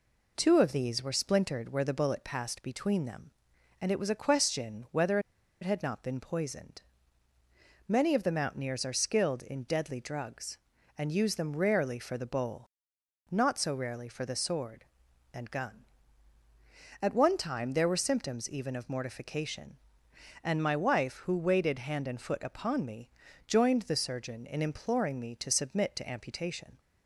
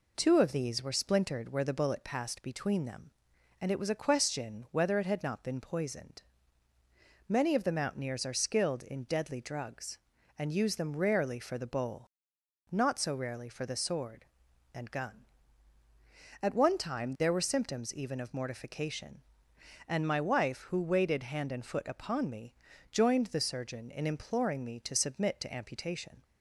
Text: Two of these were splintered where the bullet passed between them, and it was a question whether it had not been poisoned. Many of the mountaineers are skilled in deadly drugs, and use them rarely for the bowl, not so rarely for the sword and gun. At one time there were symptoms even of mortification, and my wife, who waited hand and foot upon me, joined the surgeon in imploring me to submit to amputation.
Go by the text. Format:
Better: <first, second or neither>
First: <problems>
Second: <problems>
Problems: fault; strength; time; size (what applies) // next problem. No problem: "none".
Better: second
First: pauses between "whether" and "it"; at 5.1 s; 0.42 s long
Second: none